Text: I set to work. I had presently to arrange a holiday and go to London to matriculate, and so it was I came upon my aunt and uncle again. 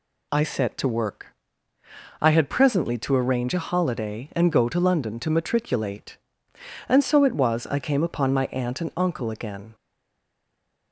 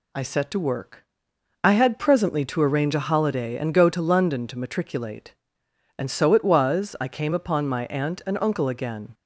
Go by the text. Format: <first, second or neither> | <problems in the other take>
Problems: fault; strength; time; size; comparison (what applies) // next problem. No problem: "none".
second | stays silent after the last word; noticeable; from 9.7 s on; 1.2 s long